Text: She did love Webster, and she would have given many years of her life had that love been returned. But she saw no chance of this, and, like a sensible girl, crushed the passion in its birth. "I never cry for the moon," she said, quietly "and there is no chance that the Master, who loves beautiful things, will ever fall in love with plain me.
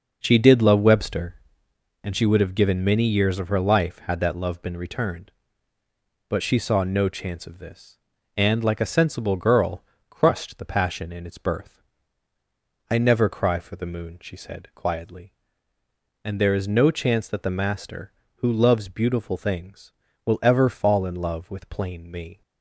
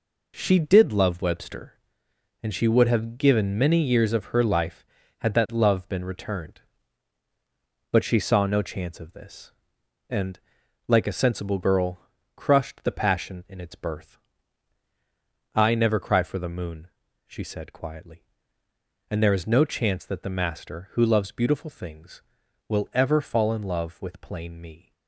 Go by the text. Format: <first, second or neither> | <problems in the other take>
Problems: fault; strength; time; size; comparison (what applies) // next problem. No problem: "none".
second | starts louder than the rest; noticeable; until 1.9 s; 6 dB